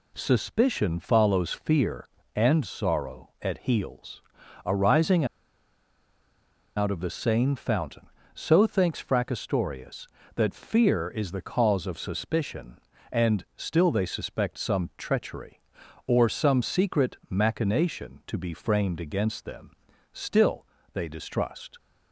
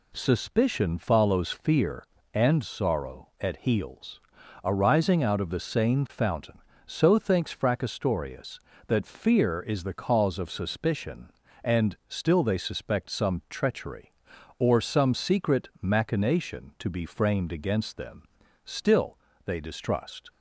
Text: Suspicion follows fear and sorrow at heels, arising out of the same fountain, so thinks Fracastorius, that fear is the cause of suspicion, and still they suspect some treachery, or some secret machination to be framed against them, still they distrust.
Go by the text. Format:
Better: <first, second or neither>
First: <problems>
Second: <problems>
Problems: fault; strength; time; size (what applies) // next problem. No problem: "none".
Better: second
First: pauses between "arising" and "out"; strong; at 5.2 s; 1.5 s long // pauses between "still" and "they"; slight; at 20.6 s; 0.26 s long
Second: pauses between "still" and "they"; slight; at 19.1 s; 0.26 s long